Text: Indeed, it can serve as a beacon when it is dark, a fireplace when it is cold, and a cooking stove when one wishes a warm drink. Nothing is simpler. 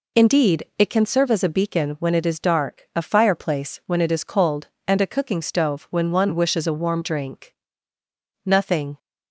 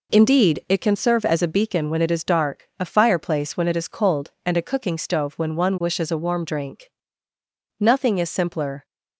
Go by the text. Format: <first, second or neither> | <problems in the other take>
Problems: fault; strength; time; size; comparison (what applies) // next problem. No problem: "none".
second | stops before "is simpler"; at 8.9 s